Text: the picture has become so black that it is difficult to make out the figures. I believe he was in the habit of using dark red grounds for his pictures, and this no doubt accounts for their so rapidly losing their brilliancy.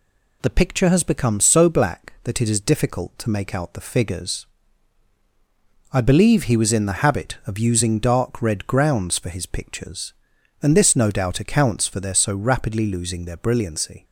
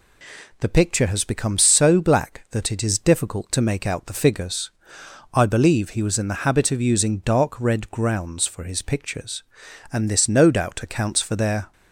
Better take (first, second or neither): first